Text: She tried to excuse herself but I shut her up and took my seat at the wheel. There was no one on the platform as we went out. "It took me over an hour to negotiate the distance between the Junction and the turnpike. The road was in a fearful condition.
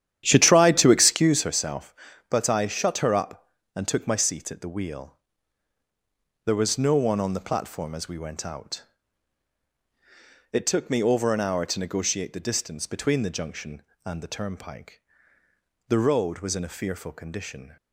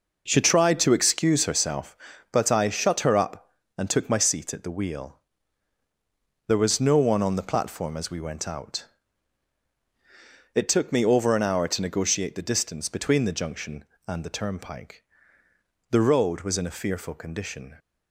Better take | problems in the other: second | starts louder than the rest; strong; until 1.4 s; 10.5 dB

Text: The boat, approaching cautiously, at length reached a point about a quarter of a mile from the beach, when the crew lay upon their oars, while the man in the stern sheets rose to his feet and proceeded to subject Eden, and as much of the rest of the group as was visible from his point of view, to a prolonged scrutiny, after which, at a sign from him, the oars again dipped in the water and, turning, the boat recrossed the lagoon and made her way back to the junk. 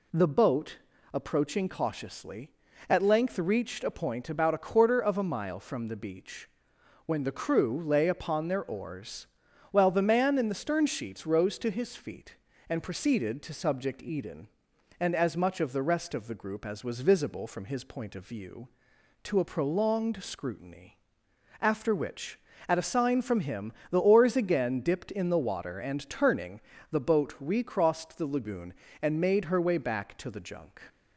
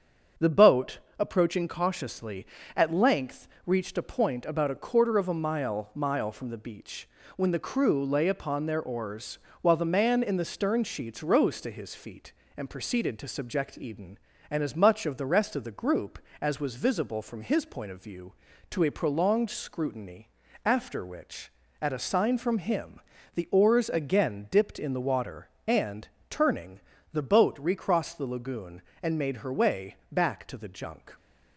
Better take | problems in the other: first | starts louder than the rest; strong; until 1.5 s; 7.5 dB // pauses between "length" and "reached"; slight; at 3.4 s; 0.18 s long // says "mile" twice; at 5.9 s // pauses between "way" and "back"; slight; at 29.9 s; 0.16 s long

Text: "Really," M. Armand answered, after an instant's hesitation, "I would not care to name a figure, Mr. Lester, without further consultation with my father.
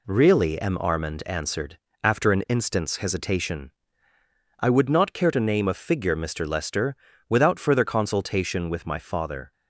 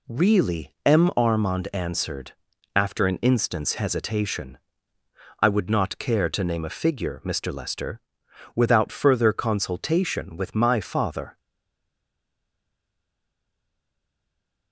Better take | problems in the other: first | stays silent after the last word; strong; from 11.3 s on; 3.4 s long

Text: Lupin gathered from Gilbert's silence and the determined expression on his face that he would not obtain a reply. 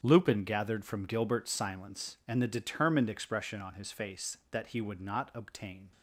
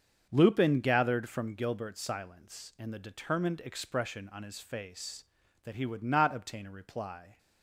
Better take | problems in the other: second | starts louder than the rest; strong; until 1.0 s; 8 dB; also in the second // stops before "a reply"; at 5.9 s

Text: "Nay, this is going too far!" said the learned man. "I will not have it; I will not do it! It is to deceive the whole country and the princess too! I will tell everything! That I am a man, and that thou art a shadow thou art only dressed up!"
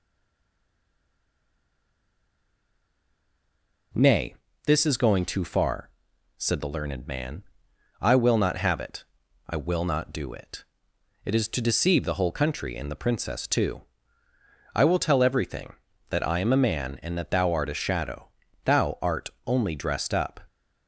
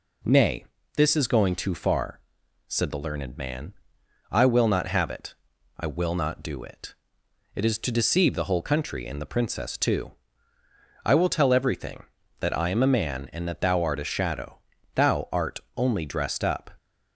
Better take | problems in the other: second | stays silent before the first word; strong; until 3.9 s; 3.9 s long // pauses between "shadow" and "thou"; slight; at 18.3 s; 0.34 s long; slight in the second // pauses between "art" and "only"; slight; at 19.2 s; 0.18 s long; slight in the second

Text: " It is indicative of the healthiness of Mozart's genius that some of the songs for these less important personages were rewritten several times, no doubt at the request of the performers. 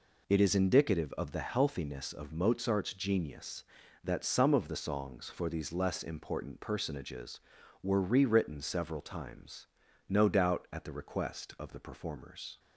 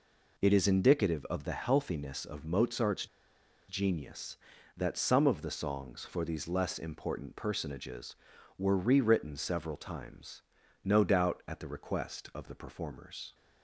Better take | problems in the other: first | pauses between "Mozart's" and "genius"; noticeable; at 3.0 s; 0.62 s long

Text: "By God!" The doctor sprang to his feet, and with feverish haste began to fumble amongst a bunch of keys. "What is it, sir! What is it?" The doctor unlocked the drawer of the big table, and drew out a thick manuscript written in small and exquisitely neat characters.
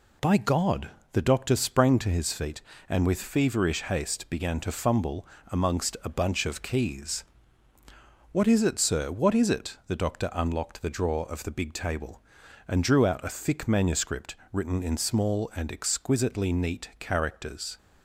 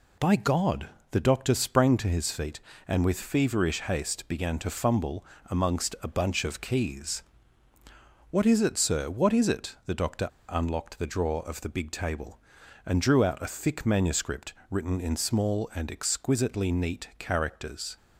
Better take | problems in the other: first | pauses between "fumble" and "amongst"; slight; at 5.2 s; 0.22 s long; slight in the first // pauses between "doctor" and "unlocked"; slight; at 10.2 s; 0.22 s long // pauses between "manuscript" and "written"; slight; at 14.5 s; 0.18 s long; slight in the first

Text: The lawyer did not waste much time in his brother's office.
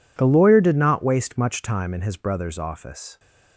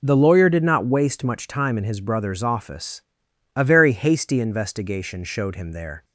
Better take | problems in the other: first | goes on to say "A very hasty investigation showed him there"; strong; from 3.5 s on; 2.5 s long

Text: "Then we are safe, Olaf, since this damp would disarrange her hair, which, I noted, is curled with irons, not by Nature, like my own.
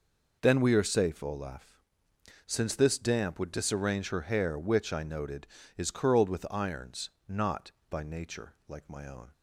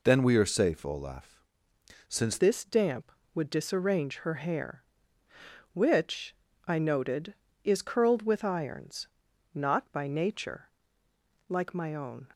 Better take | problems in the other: first | changes voice at "this"; from 2.3 s on; 9.9 s long

